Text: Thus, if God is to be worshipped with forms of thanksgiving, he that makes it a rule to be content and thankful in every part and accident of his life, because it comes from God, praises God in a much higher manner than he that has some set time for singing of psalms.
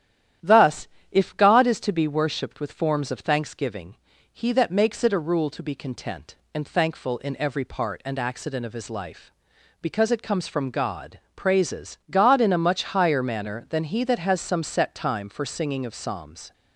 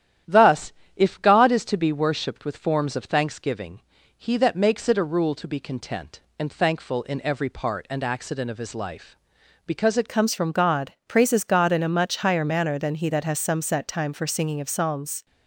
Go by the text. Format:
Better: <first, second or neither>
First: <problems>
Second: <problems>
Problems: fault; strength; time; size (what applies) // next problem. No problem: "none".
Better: first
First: starts louder than the rest; strong; until 1.6 s; 11 dB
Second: starts louder than the rest; strong; until 1.4 s; 11 dB // changes voice at "comes"; from 10.0 s on; 5.2 s long